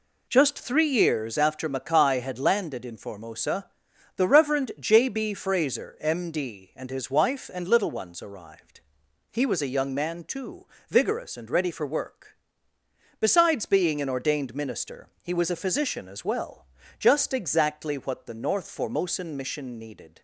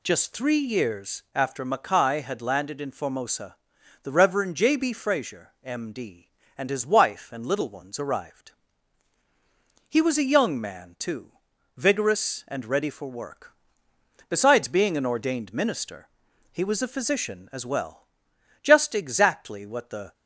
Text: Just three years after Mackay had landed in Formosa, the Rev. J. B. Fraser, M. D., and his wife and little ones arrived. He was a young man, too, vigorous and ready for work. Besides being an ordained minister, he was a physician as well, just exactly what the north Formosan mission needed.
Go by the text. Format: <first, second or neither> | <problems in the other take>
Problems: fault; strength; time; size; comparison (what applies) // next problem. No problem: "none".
first | stops before "north Formosan mission needed"; at 20.1 s